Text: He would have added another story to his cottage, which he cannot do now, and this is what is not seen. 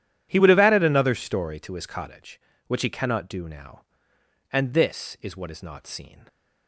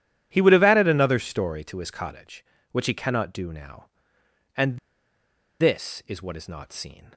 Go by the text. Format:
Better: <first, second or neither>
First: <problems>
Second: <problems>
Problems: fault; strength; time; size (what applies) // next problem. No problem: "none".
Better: first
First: none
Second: pauses between "and" and "this"; noticeable; at 4.7 s; 0.82 s long